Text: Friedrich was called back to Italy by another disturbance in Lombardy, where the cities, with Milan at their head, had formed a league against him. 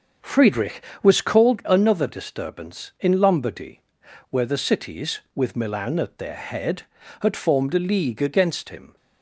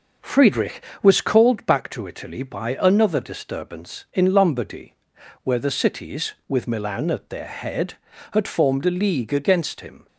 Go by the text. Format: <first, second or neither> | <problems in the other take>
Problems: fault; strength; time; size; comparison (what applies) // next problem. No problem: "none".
second | starts louder than the rest; until 1.4 s; 6.5 dB // skips "back to Italy by"; at 1.6 s